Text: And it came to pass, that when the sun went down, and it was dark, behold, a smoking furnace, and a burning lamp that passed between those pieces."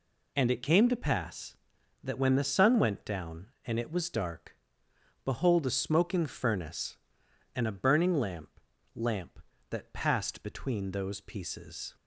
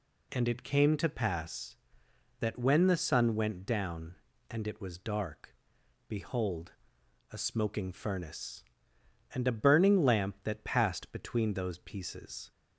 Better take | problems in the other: second | says "lamp" twice; at 8.9 s

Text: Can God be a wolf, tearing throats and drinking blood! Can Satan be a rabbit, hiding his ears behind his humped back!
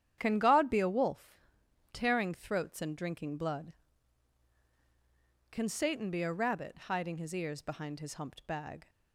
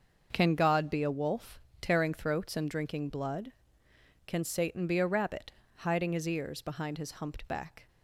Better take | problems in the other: second | starts louder than the rest; strong; until 1.1 s; 10 dB; also in the second // says "bag" for "back"; at 8.4 s

